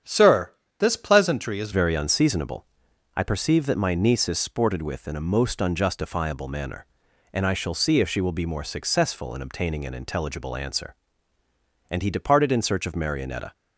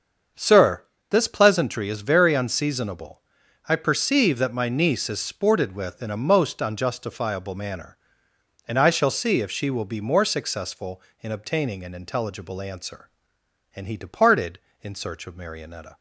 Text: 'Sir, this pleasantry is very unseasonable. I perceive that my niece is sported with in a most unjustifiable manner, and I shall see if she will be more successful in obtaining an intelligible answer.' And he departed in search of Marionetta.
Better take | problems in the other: second | starts louder than the rest; strong; until 1.3 s; 8.5 dB; also in the second // changes voice at "very"; from 1.7 s on; 11.8 s long

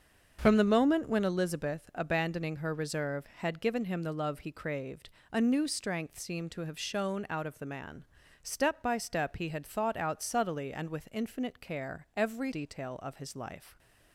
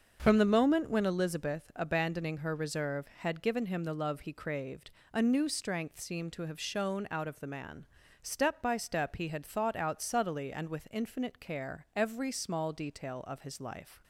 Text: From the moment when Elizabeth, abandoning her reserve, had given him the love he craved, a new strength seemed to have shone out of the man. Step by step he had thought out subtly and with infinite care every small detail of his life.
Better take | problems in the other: second | starts louder than the rest; until 1.4 s; 6.5 dB; also in the second // skips "small"; at 12.5 s

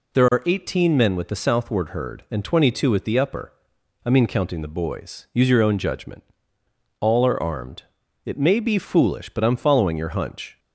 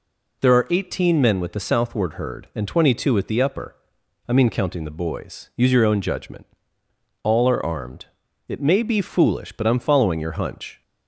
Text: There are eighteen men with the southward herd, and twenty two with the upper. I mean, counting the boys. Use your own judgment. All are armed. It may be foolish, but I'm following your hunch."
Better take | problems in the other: neither | none

